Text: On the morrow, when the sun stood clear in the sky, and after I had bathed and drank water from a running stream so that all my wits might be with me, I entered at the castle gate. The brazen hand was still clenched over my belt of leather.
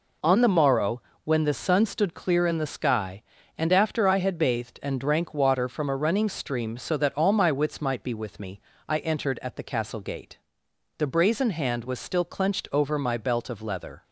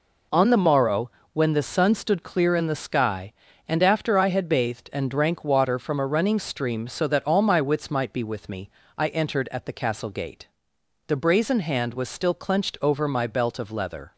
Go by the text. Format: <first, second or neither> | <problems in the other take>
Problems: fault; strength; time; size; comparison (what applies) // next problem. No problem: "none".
neither | none